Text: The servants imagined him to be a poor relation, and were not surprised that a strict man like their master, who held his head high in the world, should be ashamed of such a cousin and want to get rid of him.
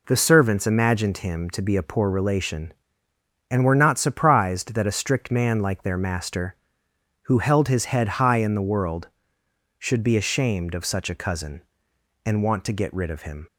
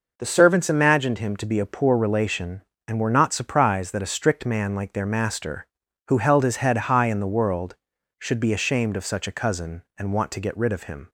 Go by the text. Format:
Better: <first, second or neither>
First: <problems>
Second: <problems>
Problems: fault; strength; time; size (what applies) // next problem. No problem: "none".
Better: neither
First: none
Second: none